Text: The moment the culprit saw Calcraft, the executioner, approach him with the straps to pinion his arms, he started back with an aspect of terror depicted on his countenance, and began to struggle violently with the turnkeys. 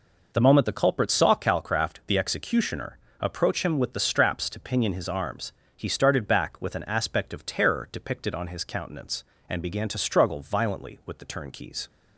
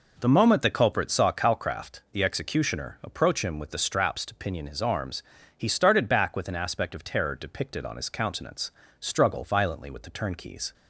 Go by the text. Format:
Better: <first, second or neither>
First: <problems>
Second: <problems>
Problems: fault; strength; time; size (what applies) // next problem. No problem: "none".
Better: first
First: none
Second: skips "and began to"; at 8.8 s